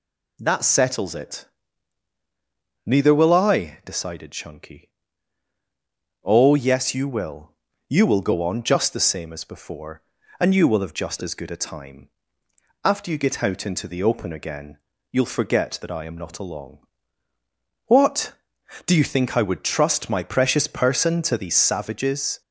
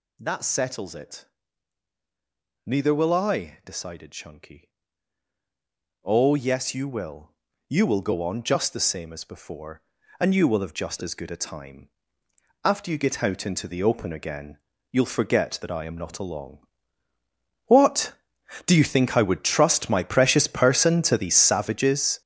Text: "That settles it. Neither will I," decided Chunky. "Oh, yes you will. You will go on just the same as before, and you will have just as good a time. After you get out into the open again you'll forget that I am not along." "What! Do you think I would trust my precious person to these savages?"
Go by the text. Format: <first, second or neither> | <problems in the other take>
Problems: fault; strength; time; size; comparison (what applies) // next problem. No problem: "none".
first | gets louder; strong; throughout; 10 dB // pauses between "again" and "you'll"; slight; at 14.5 s; 0.34 s long; slight in the first